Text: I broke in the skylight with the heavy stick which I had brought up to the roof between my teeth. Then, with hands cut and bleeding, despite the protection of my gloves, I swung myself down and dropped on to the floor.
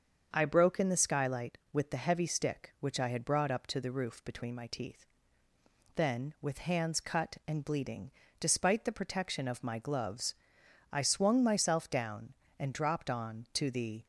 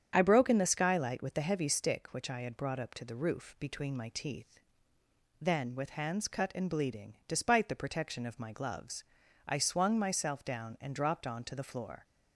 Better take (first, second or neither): second